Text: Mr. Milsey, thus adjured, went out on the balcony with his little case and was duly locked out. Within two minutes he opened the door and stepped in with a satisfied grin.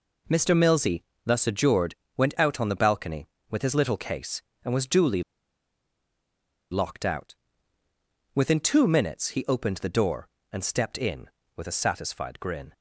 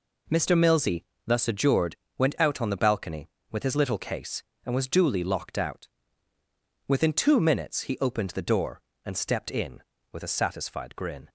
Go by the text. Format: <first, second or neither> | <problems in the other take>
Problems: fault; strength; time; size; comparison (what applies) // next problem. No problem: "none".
second | pauses between "duly" and "locked"; strong; at 5.2 s; 1.5 s long